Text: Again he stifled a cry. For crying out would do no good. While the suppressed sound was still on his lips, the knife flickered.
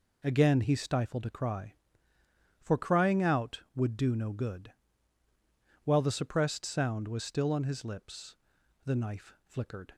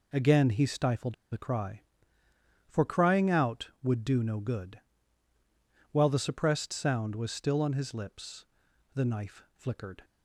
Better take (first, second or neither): first